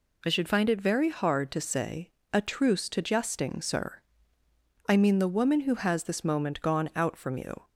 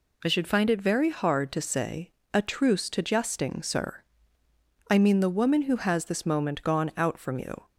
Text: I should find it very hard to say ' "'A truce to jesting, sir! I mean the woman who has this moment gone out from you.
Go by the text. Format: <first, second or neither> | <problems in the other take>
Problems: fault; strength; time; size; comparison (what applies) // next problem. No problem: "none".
neither | none